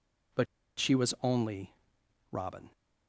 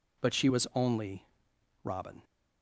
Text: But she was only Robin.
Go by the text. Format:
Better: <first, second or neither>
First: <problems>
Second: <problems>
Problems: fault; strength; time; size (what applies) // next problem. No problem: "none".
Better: second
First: pauses between "But" and "she"; slight; at 0.4 s; 0.33 s long // pauses between "only" and "Robin"; noticeable; at 1.7 s; 0.58 s long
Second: pauses between "only" and "Robin"; noticeable; at 1.2 s; 0.58 s long